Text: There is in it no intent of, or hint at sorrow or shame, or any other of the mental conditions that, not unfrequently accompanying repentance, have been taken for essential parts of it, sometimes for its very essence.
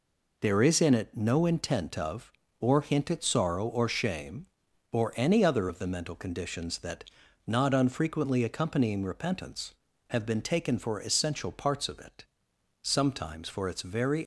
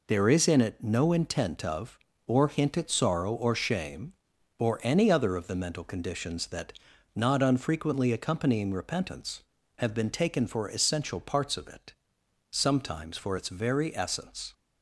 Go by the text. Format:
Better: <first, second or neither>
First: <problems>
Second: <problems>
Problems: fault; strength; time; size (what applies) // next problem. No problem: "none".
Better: second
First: stops before "essence"; at 14.2 s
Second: none